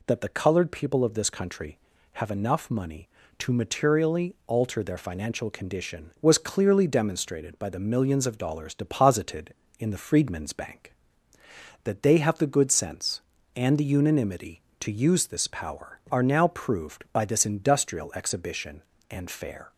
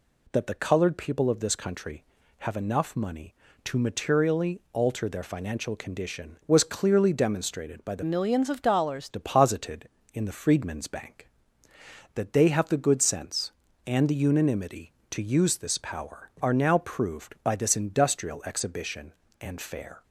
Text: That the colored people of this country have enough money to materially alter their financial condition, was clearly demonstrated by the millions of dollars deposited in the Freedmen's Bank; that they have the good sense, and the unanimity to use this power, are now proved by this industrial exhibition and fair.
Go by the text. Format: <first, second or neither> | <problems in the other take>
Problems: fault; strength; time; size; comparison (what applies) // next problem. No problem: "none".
first | changes voice from "millions" to "dollars"; from 8.0 to 9.0 s; 1.0 s long